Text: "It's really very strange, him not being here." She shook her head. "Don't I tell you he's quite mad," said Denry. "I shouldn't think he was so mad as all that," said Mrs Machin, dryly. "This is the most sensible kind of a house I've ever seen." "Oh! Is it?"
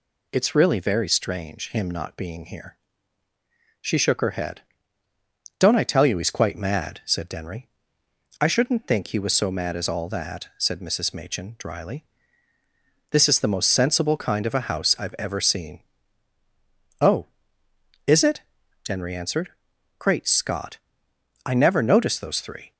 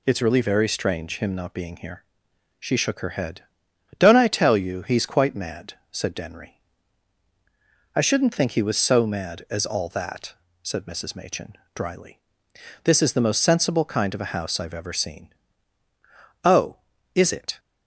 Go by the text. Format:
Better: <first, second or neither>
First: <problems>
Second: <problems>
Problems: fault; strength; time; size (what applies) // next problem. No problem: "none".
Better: second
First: goes on to say "Denry answered Great Scott I never noticed those three"; strong; from 18.8 s on; 3.8 s long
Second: none